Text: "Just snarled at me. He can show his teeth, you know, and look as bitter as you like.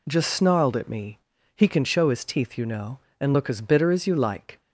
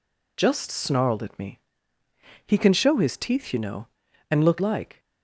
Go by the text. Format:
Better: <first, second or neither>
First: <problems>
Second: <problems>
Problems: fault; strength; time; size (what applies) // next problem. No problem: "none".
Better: first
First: none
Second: skips "as bitter as you"; at 4.5 s